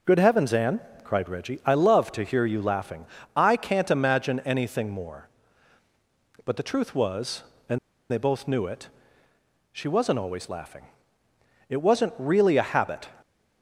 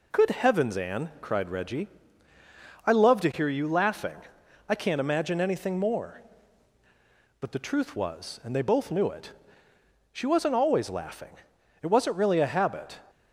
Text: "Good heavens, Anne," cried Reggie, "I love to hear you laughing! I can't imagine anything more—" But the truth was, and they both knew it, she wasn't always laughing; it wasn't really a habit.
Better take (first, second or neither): second